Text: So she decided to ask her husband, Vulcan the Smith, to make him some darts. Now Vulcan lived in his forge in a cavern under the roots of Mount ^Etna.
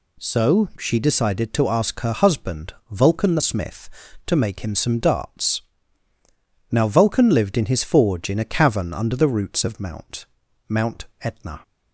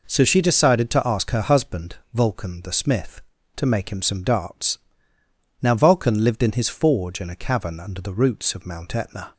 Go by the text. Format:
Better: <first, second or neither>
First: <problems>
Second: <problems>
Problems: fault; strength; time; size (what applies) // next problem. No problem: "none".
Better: second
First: says "Mount" twice; at 10.6 s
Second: none